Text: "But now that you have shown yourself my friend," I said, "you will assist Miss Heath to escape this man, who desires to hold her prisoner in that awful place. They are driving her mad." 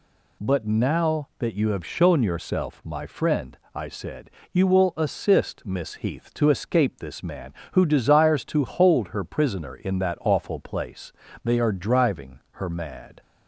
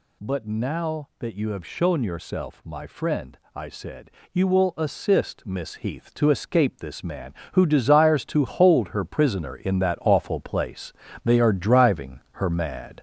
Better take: first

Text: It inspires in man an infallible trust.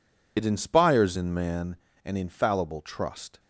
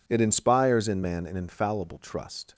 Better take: second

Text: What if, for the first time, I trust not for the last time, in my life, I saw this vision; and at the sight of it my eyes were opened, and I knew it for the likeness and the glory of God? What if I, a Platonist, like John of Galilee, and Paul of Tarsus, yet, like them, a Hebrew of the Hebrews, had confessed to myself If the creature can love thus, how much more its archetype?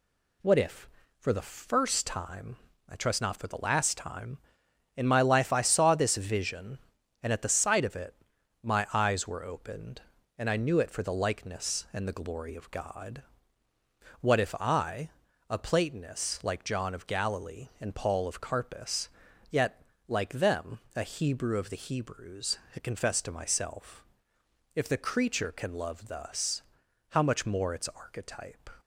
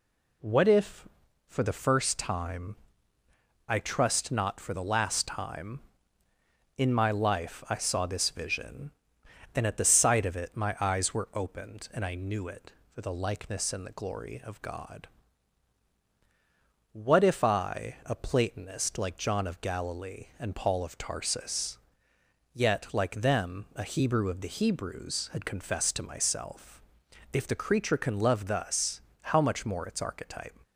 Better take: second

